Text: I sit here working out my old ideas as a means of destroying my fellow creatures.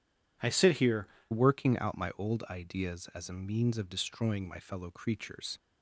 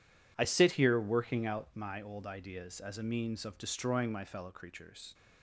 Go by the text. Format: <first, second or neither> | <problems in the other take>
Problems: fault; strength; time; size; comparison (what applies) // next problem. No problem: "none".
second | changes voice at "working"; from 1.3 s on; 4.2 s long